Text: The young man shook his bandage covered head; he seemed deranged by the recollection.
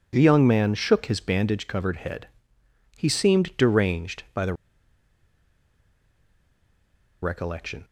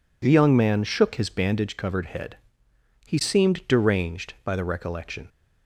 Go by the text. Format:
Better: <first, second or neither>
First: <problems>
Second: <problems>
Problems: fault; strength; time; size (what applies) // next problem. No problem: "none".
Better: second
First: pauses between "the" and "recollection"; strong; at 4.5 s; 2.6 s long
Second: none